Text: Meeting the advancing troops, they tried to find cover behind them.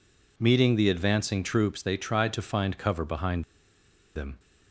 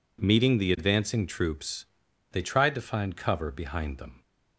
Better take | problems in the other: second | pauses between "behind" and "them"; noticeable; at 3.4 s; 0.73 s long

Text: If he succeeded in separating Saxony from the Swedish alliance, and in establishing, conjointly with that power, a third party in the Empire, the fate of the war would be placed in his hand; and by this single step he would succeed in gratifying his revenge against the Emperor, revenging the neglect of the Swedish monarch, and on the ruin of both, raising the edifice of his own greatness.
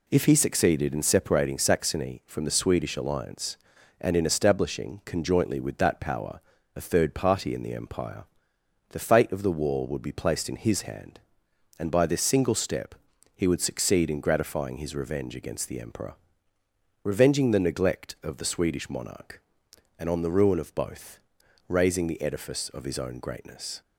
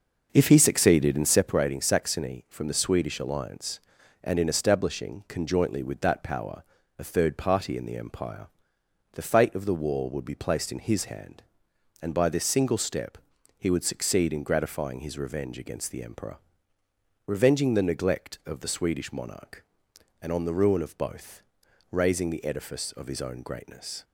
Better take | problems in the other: first | starts louder than the rest; noticeable; until 1.5 s; 6 dB // pauses between "step" and "he"; at 13.1 s; 0.40 s long; also in the first

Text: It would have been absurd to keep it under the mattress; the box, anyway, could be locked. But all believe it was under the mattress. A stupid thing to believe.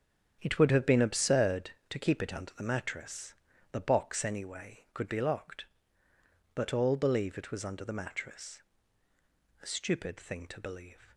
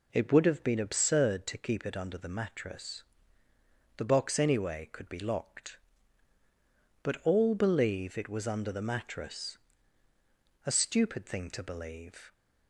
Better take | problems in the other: second | gets quieter; strong; throughout; 10.5 dB

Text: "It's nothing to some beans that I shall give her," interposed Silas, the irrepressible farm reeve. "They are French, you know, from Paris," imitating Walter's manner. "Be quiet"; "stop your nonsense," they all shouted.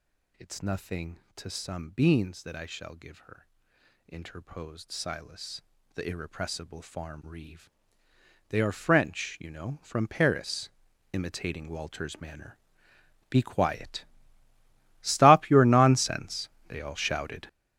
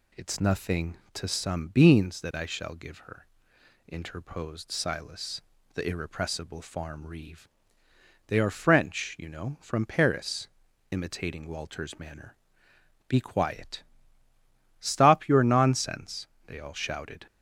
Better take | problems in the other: second | gets louder; strong; throughout; 11.5 dB

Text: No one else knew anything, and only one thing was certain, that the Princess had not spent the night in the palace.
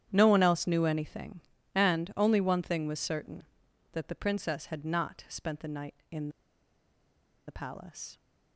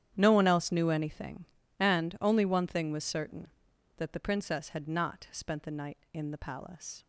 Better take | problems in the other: second | starts louder than the rest; strong; until 1.1 s; 10 dB; strong in the second // pauses between "in" and "the"; at 6.2 s; 1.1 s long

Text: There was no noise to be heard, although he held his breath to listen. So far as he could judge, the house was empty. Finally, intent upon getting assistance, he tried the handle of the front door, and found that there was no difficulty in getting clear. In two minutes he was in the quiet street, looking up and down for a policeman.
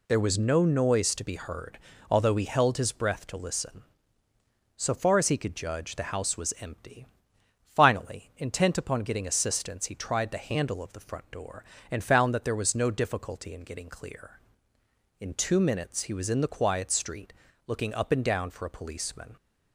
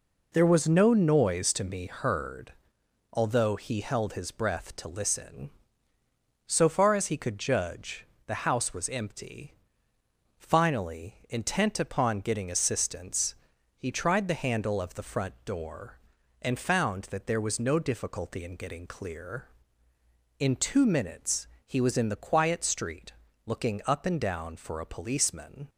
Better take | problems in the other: first | says "me" for "be"; at 1.6 s // pauses between "minutes" and "he"; slight; at 21.4 s; 0.20 s long

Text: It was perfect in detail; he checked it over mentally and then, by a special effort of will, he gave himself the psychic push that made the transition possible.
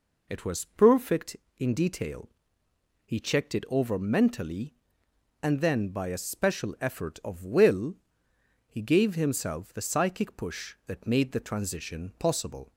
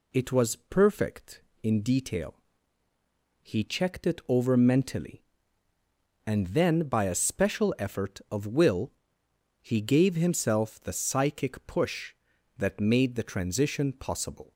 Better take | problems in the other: neither | none

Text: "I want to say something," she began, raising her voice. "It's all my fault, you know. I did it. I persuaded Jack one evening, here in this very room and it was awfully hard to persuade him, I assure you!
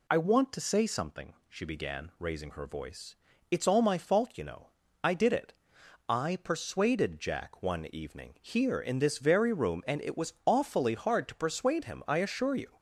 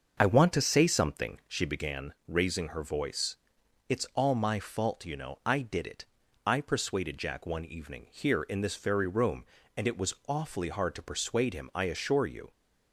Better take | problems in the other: first | starts louder than the rest; until 2.0 s; 6 dB

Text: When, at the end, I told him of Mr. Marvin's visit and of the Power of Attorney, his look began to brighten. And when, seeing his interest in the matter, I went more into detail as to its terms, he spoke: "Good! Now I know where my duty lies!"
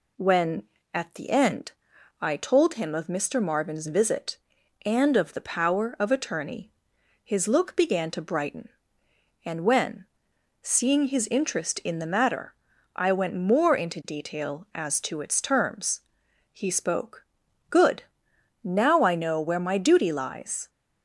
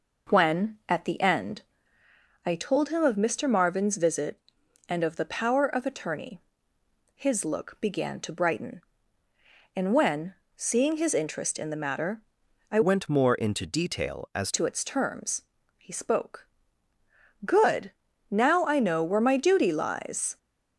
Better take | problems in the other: first | changes voice from "went" to "as"; from 12.8 to 14.5 s; 1.7 s long

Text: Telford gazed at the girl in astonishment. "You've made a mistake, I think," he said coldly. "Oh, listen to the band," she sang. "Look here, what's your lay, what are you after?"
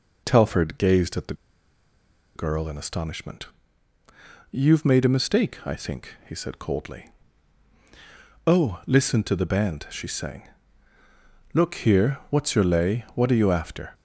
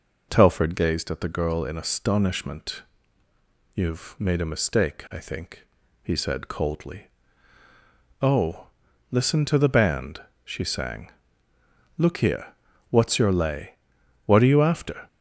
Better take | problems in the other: second | pauses between "the" and "girl"; at 1.3 s; 1.0 s long

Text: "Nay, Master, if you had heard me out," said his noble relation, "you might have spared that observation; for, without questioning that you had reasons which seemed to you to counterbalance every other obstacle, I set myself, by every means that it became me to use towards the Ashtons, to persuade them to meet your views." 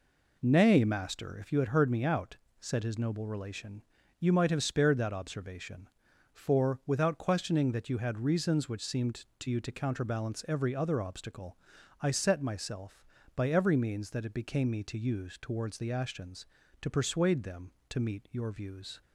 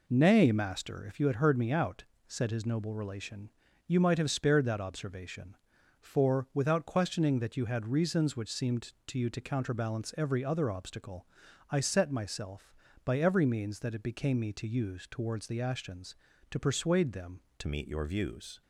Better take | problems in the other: first | changes voice at "meet"; from 17.6 s on; 1.0 s long

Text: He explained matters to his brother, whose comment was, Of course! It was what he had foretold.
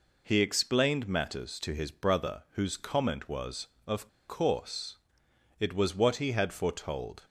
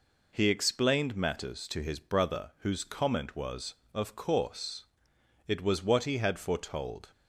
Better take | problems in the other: second | pauses between "Of" and "course"; slight; at 4.0 s; 0.21 s long

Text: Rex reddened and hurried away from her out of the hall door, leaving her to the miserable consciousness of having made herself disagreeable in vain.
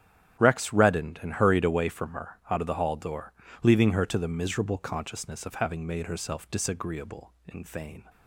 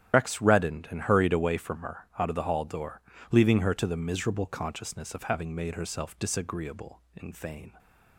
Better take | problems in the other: first | loses the start of "Rex"; at 0.1 s; 55 ms // starts louder than the rest; strong; until 1.2 s; 11 dB; strong in the first

